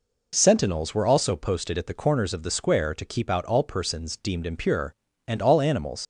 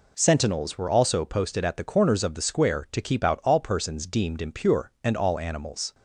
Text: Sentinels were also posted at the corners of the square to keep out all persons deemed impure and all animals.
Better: second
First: leaves "animals" unfinished; at 6.0 s; 90 ms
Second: none

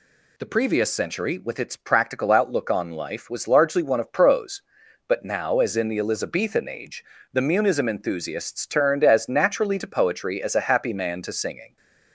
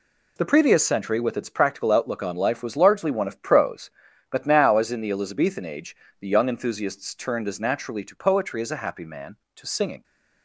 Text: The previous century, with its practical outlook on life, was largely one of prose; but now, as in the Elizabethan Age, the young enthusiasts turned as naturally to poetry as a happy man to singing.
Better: second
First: says "munism" for "young"; at 7.4 s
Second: none

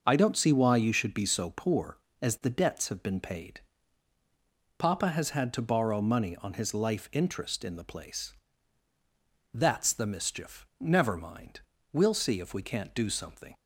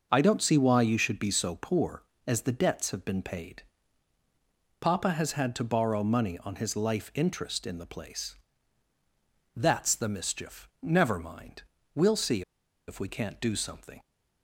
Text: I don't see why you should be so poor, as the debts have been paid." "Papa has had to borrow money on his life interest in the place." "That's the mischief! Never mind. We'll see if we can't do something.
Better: first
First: starts louder than the rest; noticeable; until 1.0 s; 6 dB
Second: starts louder than the rest; noticeable; until 1.1 s; 6 dB // pauses between "see" and "if"; noticeable; at 12.4 s; 0.46 s long

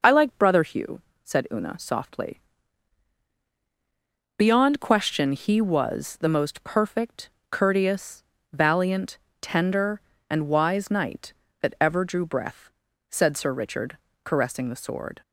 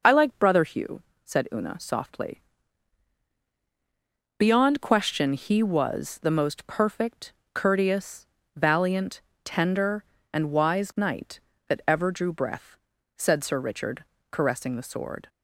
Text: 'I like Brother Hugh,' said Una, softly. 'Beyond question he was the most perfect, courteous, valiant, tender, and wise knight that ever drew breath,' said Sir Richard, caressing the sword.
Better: neither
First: none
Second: none

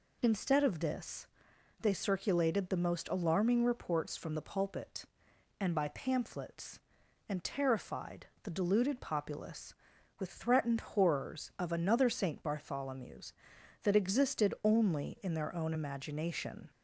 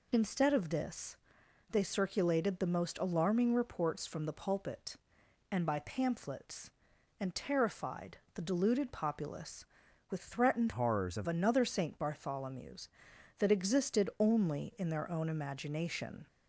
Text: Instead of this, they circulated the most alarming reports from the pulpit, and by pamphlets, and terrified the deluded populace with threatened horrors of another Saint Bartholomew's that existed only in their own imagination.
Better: first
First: pauses between "terrified" and "the"; slight; at 8.2 s; 0.18 s long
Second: pauses between "terrified" and "the"; slight; at 8.1 s; 0.18 s long // changes voice from "horrors" to "of"; from 10.7 to 11.2 s; 0.5 s long

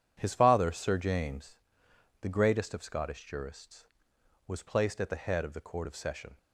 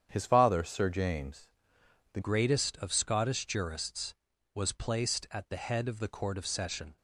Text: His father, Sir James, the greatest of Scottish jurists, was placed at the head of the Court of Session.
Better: first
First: none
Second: starts louder than the rest; strong; until 1.1 s; 8.5 dB // changes voice at "greatest"; from 2.2 s on; 4.7 s long

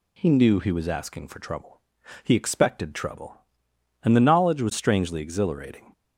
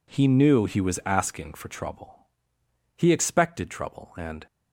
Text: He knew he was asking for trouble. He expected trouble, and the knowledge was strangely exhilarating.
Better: first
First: none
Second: stops before "the knowledge was strangely exhilarating"; at 4.4 s

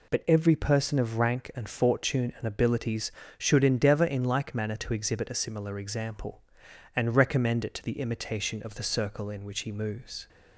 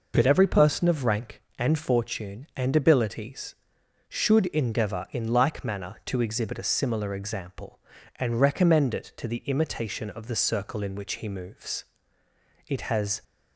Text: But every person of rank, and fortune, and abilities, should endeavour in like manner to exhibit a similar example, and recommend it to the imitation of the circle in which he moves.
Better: first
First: none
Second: goes on to say "It has"; from 12.6 s on; 0.54 s long

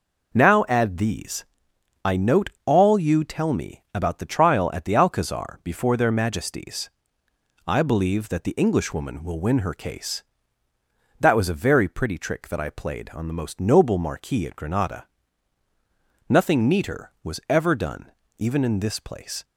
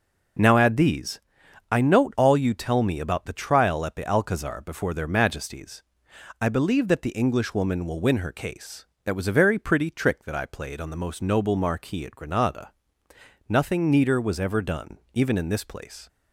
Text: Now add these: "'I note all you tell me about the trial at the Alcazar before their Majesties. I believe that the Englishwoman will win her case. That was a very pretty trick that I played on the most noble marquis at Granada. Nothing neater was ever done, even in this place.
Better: neither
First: none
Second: none

